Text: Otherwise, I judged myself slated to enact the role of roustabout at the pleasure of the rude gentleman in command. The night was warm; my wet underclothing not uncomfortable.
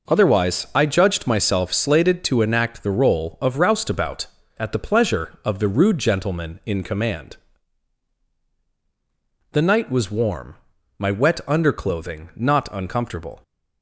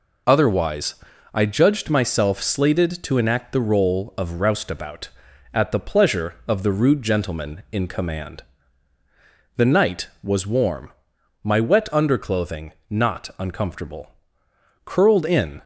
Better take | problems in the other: first | pauses between "underclothing" and "not"; slight; at 12.7 s; 0.16 s long // goes on to say "Curled in"; noticeable; from 14.8 s on; 0.78 s long

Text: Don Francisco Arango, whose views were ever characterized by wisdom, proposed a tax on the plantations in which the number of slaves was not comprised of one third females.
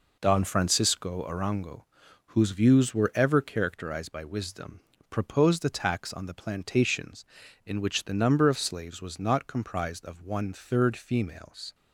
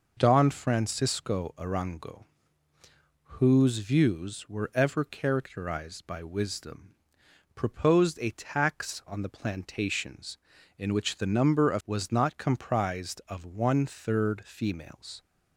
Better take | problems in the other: first | skips "slaves"; at 11.8 s

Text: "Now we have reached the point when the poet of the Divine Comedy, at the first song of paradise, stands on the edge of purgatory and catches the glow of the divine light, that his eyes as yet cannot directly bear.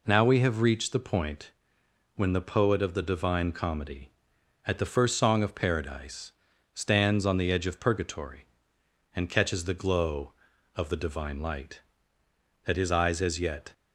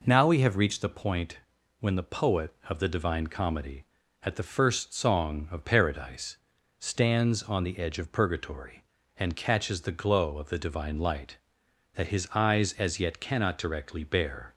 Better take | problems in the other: second | pauses between "point" and "when"; noticeable; at 1.5 s; 0.64 s long; also in the second // stops before "cannot directly bear"; at 13.7 s

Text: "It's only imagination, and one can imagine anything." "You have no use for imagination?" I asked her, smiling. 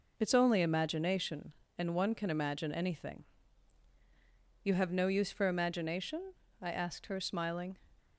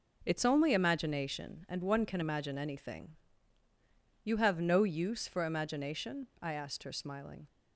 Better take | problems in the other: neither | none

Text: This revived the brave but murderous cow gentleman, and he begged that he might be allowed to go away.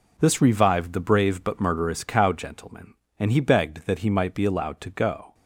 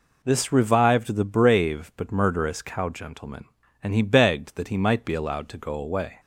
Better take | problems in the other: second | stops before "away"; at 5.3 s

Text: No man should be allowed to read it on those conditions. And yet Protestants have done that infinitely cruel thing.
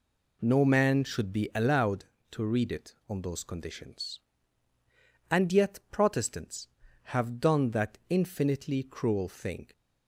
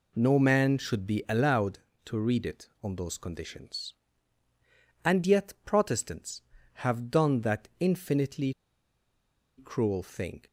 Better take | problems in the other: first | pauses between "infinitely" and "cruel"; at 8.5 s; 1.0 s long

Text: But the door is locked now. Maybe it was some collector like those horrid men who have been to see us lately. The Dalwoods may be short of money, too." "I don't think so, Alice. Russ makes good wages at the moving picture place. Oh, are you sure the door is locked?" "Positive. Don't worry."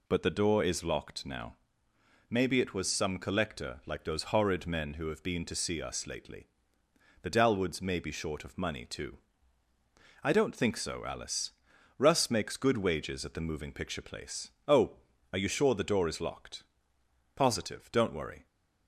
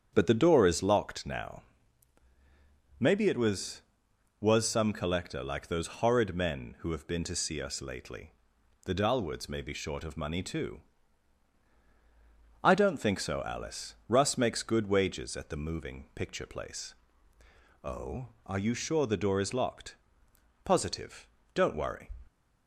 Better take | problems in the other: first | starts louder than the rest; strong; until 1.1 s; 8 dB // says "was" twice; at 4.3 s

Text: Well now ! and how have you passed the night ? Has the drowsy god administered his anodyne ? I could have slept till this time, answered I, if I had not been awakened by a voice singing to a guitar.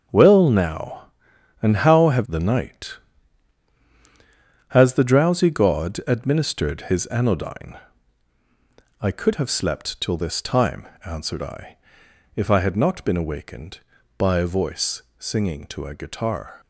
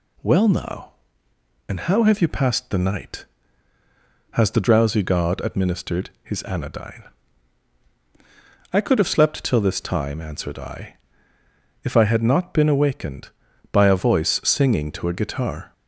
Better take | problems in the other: second | starts louder than the rest; until 1.7 s; 7 dB // skips "you passed"; at 2.2 s // pauses between "voice" and "singing"; slight; at 15.0 s; 0.16 s long

